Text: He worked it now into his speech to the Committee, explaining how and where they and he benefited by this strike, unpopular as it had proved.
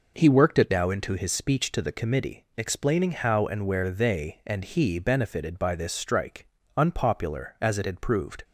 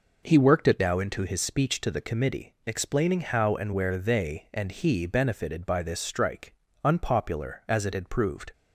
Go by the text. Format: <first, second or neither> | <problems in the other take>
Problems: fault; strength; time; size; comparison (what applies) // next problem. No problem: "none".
neither | none